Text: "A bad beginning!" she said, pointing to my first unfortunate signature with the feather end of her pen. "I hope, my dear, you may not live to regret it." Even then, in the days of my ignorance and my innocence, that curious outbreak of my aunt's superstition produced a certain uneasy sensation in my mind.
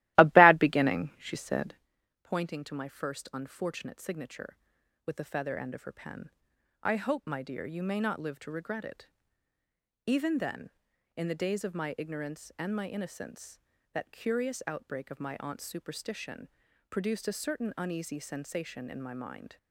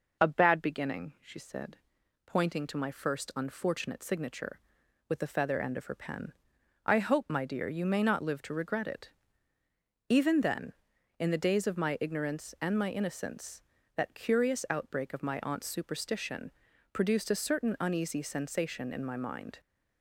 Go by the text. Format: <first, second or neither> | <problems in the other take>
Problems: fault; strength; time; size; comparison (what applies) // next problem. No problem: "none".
second | starts louder than the rest; strong; until 1.9 s; 16.5 dB // pauses between "superstition" and "produced"; at 16.4 s; 0.40 s long; also in the second